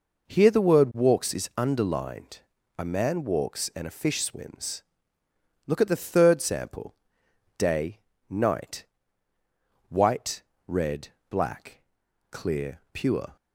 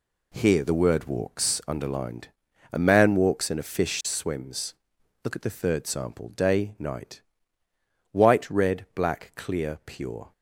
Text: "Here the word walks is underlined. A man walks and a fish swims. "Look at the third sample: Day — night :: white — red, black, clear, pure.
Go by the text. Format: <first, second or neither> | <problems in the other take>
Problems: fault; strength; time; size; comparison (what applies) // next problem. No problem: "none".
first | skips "is"; at 1.6 s